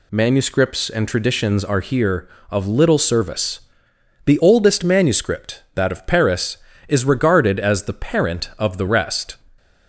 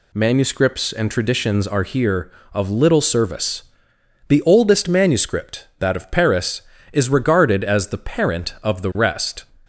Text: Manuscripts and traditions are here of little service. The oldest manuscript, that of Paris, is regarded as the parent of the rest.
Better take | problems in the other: neither | none

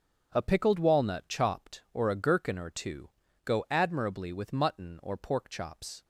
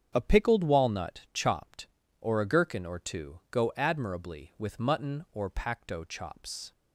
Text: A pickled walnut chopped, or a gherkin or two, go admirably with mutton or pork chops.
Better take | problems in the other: first | starts louder than the rest; strong; until 1.1 s; 8 dB; also in the first // says "pacto" for "pork"; at 5.4 s

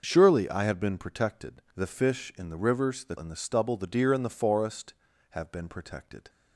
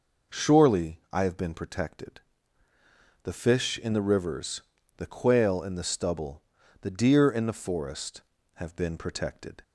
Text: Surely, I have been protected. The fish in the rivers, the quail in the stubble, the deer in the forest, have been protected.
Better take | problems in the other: second | starts louder than the rest; noticeable; until 1.0 s; 6 dB // skips "quail"; at 3.1 s

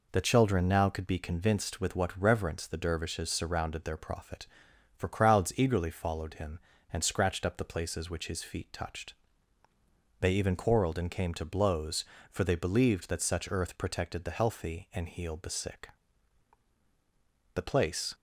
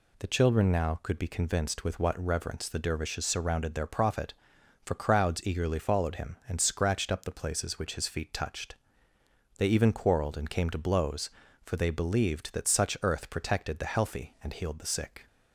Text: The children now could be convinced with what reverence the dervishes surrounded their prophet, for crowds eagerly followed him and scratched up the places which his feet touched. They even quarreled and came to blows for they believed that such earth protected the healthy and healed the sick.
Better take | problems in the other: second | goes on to say "The place"; from 17.5 s on; 0.58 s long

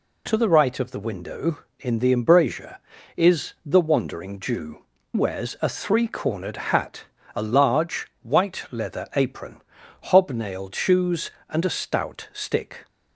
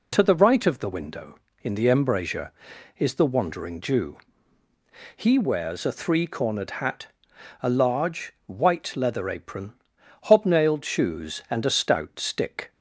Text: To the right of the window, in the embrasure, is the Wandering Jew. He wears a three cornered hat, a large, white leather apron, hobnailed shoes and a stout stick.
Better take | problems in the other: second | skips "He"; at 4.9 s

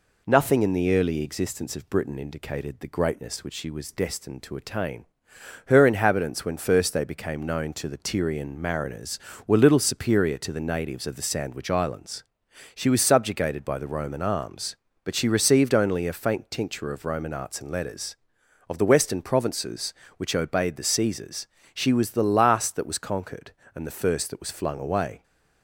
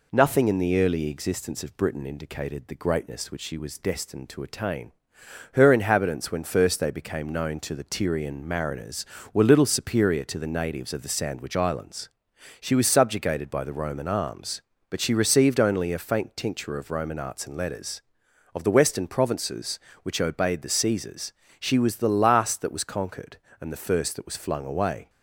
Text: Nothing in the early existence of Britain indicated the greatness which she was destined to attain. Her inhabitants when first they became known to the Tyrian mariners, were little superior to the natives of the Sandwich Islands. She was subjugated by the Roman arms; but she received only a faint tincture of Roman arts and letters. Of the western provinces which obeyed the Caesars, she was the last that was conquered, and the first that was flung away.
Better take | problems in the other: neither | none

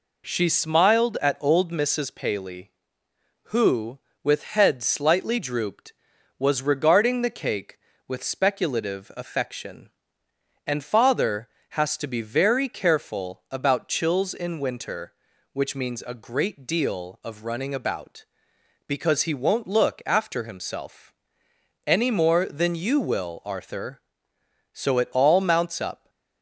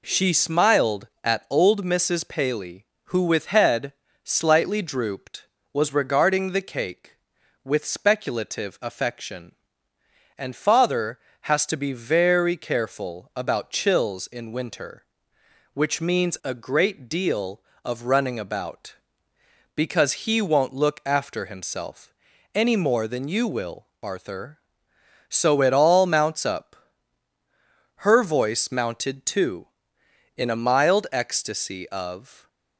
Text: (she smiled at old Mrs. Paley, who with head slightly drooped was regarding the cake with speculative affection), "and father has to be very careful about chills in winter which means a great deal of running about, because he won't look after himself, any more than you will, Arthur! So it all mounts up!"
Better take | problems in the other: first | pauses between "head" and "slightly"; slight; at 3.9 s; 0.28 s long // goes on to say "Her voice mounted too in a mild ecstasy of"; strong; from 27.9 s on; 4.5 s long

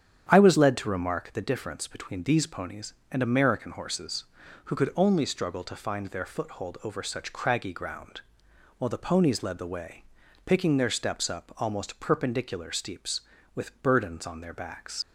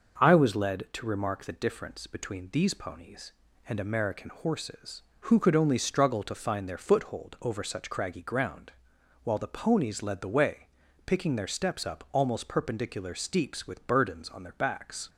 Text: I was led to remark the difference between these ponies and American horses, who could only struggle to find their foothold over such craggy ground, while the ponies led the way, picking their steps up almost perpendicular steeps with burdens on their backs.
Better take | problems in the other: second | starts louder than the rest; strong; until 1.3 s; 8.5 dB // leaves "backs" unfinished; at 15.0 s; 75 ms

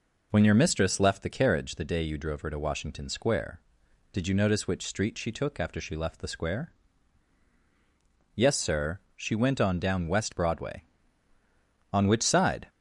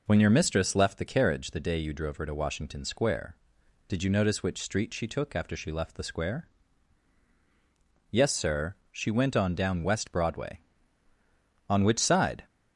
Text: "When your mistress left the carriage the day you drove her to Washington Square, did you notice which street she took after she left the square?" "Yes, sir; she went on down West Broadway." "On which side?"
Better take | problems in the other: neither | none

